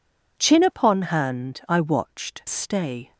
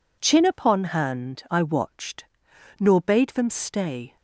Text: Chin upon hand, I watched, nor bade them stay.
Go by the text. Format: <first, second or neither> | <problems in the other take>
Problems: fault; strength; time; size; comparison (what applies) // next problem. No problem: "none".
second | skips "nor bade them"; at 2.4 s